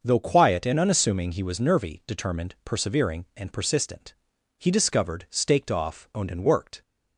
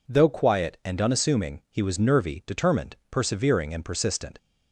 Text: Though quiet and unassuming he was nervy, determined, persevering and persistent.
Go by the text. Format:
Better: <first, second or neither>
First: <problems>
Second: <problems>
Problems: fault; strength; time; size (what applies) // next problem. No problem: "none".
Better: second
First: starts louder than the rest; until 1.0 s; 6 dB // goes on to say "He discovered staked off owned and worked"; strong; from 4.5 s on; 2.2 s long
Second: none